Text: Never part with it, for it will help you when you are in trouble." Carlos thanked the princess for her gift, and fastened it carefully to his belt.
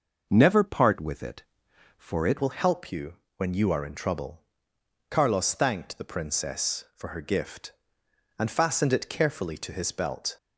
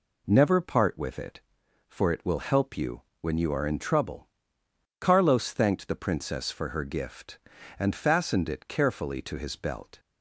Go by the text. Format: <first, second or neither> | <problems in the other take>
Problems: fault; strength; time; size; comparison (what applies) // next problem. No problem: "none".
second | changes voice at "will"; from 2.4 s on; 7.9 s long // pauses between "you" and "when"; slight; at 3.1 s; 0.22 s long; slight in the second